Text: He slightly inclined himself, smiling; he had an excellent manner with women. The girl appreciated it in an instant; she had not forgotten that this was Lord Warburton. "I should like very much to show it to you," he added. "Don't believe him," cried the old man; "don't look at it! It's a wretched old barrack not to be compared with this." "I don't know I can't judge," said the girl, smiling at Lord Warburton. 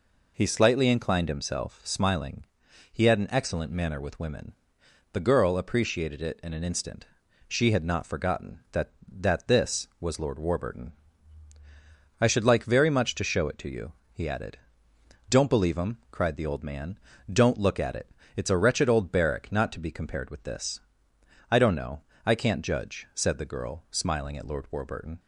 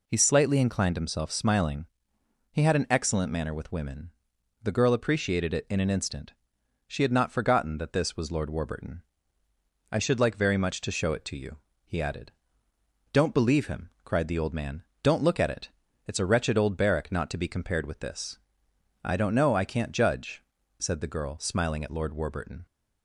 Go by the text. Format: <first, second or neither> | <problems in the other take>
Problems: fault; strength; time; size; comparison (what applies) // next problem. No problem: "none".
second | says "that" twice; at 9.0 s // pauses between "know" and "I"; slight; at 22.0 s; 0.24 s long